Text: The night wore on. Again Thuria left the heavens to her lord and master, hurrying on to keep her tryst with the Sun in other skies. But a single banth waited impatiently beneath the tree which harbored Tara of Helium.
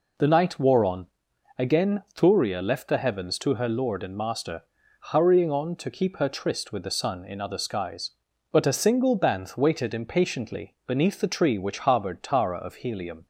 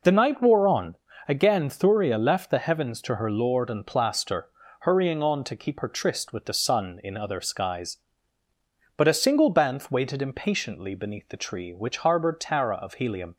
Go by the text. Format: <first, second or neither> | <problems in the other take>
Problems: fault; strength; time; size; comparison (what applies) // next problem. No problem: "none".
first | says "plaster" for "master"; at 3.8 s